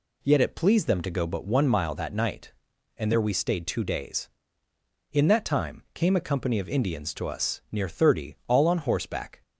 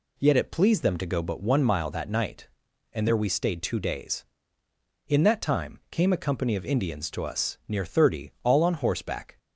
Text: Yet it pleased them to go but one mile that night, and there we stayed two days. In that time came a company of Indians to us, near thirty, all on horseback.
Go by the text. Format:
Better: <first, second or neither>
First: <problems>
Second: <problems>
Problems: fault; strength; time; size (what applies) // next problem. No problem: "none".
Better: neither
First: none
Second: none